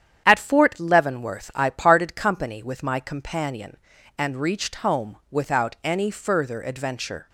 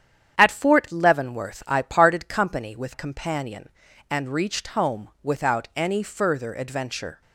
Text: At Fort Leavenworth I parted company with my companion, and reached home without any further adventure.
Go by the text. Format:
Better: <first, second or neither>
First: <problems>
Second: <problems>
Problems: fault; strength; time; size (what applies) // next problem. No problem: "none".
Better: first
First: starts louder than the rest; strong; until 1.2 s; 9 dB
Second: starts louder than the rest; strong; until 1.4 s; 9 dB // skips "my"; at 2.9 s